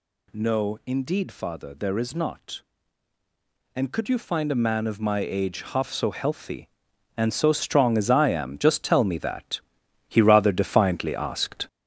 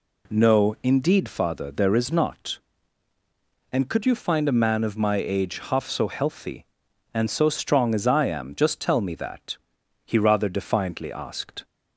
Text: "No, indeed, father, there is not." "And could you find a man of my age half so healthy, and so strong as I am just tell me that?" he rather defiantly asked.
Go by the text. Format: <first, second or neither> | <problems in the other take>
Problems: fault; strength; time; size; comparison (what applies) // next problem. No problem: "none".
second | gets louder; noticeable; throughout; 5.5 dB